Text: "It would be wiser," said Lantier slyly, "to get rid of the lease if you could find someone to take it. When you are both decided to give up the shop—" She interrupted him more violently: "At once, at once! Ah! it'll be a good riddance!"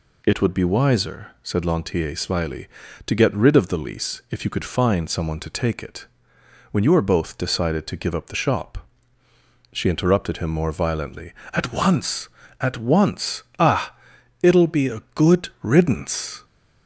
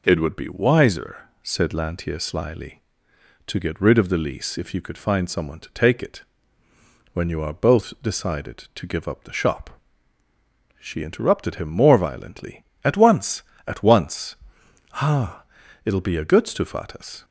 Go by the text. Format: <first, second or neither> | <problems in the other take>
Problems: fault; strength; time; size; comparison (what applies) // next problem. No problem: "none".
first | says "stufatas" for "riddance"; at 16.4 s